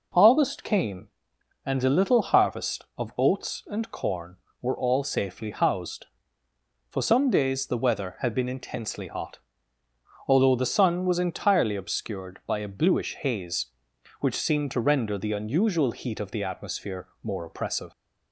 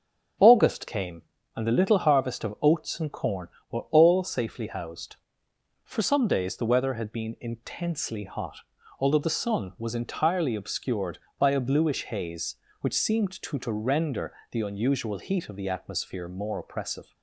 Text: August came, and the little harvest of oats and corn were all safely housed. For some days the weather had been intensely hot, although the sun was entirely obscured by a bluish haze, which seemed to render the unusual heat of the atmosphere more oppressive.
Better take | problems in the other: first | starts louder than the rest; strong; until 1.7 s; 8 dB // says "to" twice; at 13.5 s // pauses between "render" and "the"; slight; at 14.3 s; 0.18 s long

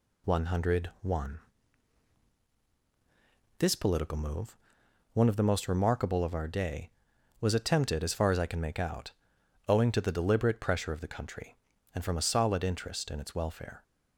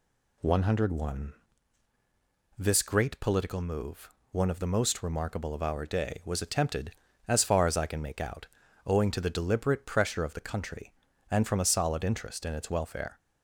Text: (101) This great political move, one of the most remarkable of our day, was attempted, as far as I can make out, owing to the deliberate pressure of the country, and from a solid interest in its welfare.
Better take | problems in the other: second | skips "great"; at 3.7 s

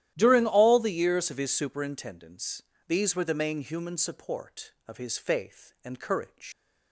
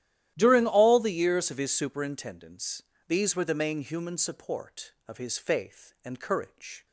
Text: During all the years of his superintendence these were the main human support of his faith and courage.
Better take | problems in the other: second | starts louder than the rest; strong; until 1.1 s; 12.5 dB; strong in the second // pauses between "superintendence" and "these"; slight; at 2.6 s; 0.26 s long; slight in the second // leaves "courage" unfinished; at 6.5 s; 130 ms

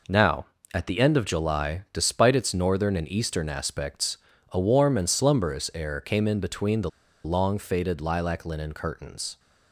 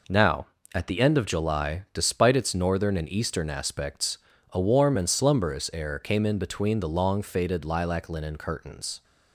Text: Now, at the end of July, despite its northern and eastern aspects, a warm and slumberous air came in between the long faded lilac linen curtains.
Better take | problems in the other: second | pauses between "the" and "long"; slight; at 6.8 s; 0.35 s long

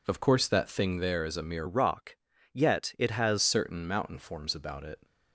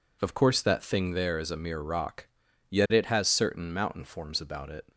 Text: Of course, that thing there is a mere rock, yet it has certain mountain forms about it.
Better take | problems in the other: second | changes voice from "rock" to "has"; from 1.6 to 3.3 s; 1.7 s long

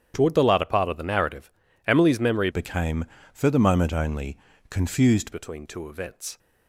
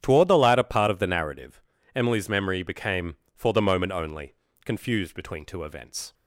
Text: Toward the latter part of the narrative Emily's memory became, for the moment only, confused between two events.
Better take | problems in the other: second | starts louder than the rest; strong; until 1.1 s; 9 dB; strong in the second // pauses between "narrative" and "Emily's"; slight; at 1.5 s; 0.34 s long; slight in the second // changes voice from "became" to "confused"; from 2.5 to 5.3 s; 2.8 s long

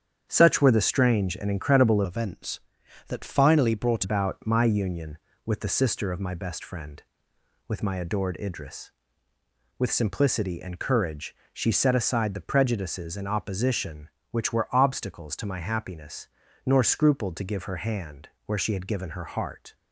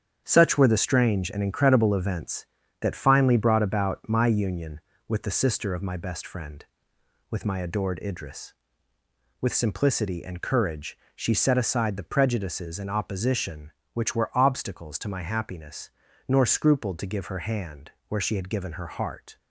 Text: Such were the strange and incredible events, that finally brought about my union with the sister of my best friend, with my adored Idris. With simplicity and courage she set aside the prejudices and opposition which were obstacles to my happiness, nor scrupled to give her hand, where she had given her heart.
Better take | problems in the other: second | starts louder than the rest; strong; until 1.2 s; 8.5 dB; strong in the second // changes voice from "events" to "brought"; from 2.0 to 4.0 s; 2.0 s long // pauses between "courage" and "she"; slight; at 11.3 s; 0.20 s long; slight in the second

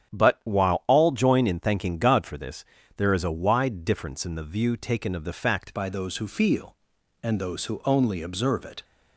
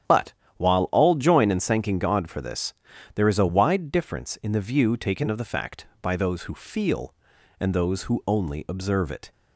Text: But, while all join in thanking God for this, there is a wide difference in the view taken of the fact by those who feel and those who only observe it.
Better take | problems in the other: second | starts louder than the rest; strong; until 1.1 s; 8.5 dB; strong in the second // changes voice at "by"; from 5.7 s on; 3.1 s long

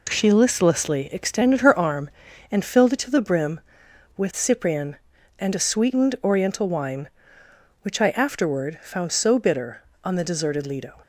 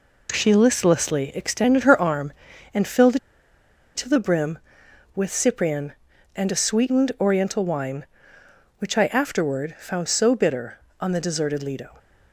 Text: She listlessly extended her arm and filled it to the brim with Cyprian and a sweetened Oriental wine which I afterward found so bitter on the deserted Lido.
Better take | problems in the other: first | pauses between "filled" and "it"; noticeable; at 3.1 s; 0.78 s long

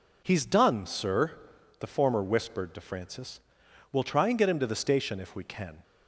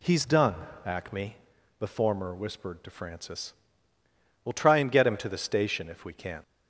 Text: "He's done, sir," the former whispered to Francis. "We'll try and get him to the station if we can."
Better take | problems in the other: first | says "acme" for "sir"; at 0.8 s

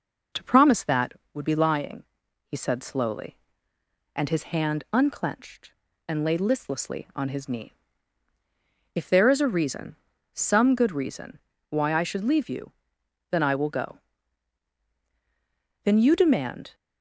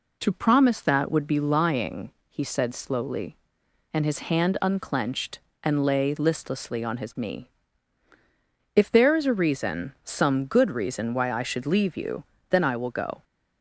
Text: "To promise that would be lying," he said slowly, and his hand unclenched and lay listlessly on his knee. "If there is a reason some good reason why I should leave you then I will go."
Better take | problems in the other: second | pauses between "reason" and "some"; slight; at 9.9 s; 0.36 s long // pauses between "reason" and "why"; slight; at 11.3 s; 0.30 s long // pauses between "you" and "then"; noticeable; at 12.7 s; 0.60 s long; slight in the second // goes on to say "Then you demand"; noticeable; from 15.8 s on; 0.92 s long

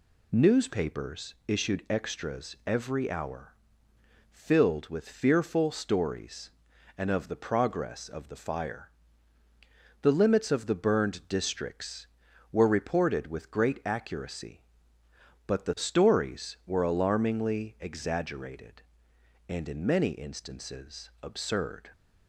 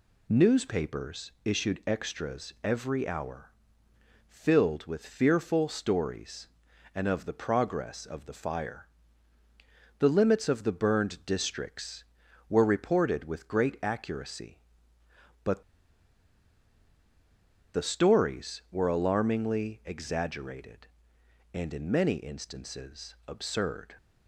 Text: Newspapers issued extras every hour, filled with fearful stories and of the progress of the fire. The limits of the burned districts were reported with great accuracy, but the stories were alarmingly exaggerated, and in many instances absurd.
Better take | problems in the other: first | pauses between "but" and "the"; strong; at 15.6 s; 2.1 s long

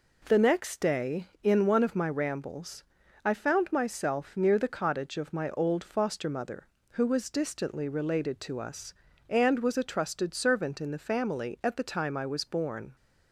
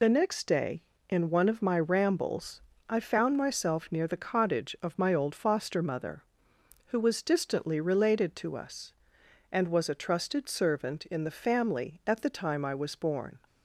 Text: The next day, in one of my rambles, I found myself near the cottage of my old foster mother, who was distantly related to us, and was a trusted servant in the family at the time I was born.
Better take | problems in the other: first | loses the start of "The"; at 0.0 s; 60 ms

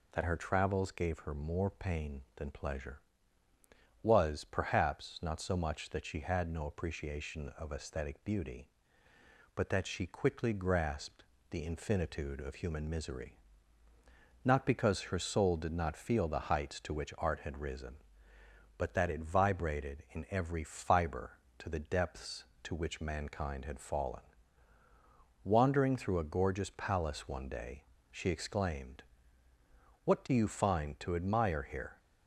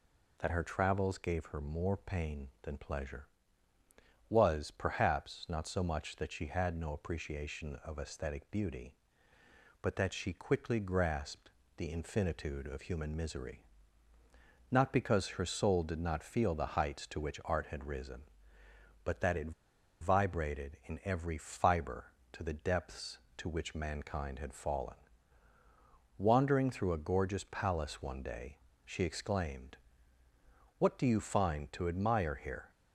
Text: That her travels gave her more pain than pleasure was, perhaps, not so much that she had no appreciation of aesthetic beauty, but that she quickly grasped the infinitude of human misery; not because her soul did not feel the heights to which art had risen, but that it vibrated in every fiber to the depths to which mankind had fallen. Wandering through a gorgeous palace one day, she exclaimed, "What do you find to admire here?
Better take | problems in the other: first | pauses between "grasped" and "the"; slight; at 11.5 s; 0.26 s long; slight in the first // pauses between "it" and "vibrated"; noticeable; at 19.5 s; 0.49 s long

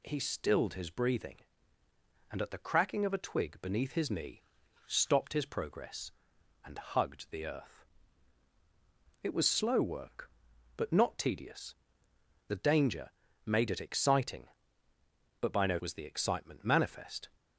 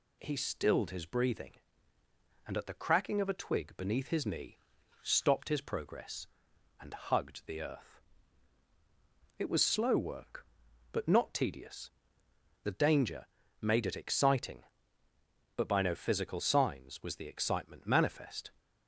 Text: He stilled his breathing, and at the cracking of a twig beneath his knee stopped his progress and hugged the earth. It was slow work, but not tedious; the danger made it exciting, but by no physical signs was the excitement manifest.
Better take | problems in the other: second | pauses between "knee" and "stopped"; at 4.4 s; 0.44 s long; also in the second // pauses between "danger" and "made"; slight; at 13.1 s; 0.34 s long; slight in the second // skips "physical signs"; at 15.7 s

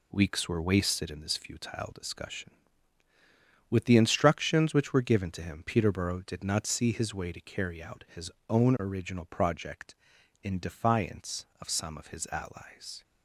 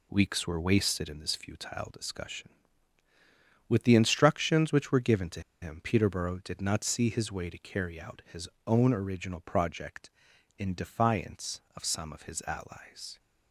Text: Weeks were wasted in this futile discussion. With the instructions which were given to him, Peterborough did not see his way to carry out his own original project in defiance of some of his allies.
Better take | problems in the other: first | pauses between "to" and "him"; slight; at 5.4 s; 0.20 s long // pauses between "his" and "own"; slight; at 8.4 s; 0.20 s long; slight in the first

